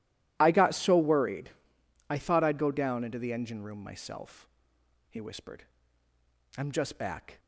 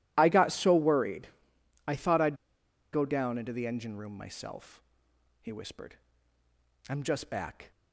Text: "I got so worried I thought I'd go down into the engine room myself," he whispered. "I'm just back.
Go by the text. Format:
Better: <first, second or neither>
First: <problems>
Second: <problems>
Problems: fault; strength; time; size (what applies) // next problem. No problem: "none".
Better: first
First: pauses between "worried" and "I"; noticeable; at 1.5 s; 0.58 s long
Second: pauses between "worried" and "I"; noticeable; at 1.2 s; 0.58 s long // pauses between "I'd" and "go"; noticeable; at 2.3 s; 0.56 s long